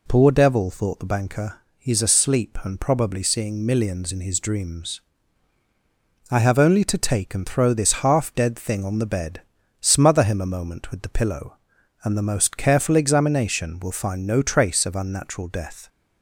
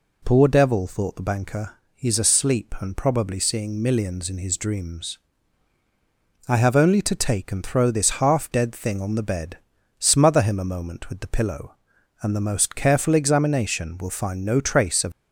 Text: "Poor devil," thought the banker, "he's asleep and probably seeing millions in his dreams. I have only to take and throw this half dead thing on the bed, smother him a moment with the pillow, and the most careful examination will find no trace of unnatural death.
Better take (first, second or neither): first